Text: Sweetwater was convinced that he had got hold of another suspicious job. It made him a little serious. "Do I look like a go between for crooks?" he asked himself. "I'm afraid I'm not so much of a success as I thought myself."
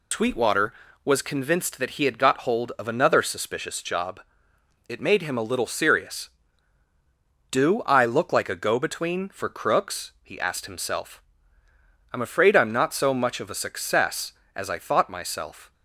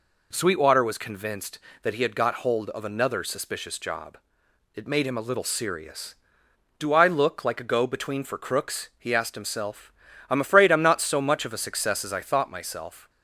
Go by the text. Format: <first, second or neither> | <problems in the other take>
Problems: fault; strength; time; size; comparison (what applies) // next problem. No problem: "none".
second | loses the start of "Sweetwater"; at 0.1 s; 140 ms